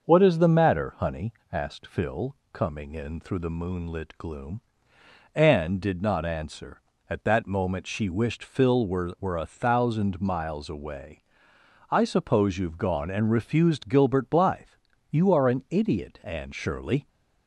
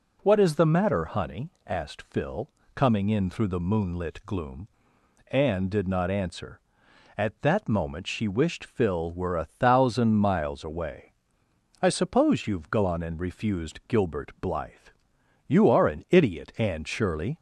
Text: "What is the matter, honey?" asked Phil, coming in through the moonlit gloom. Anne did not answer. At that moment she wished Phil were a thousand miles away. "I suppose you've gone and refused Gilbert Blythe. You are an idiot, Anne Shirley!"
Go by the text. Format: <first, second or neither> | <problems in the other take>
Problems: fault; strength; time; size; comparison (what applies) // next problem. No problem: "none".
second | starts louder than the rest; until 1.0 s; 6.5 dB // says "were" twice; at 9.2 s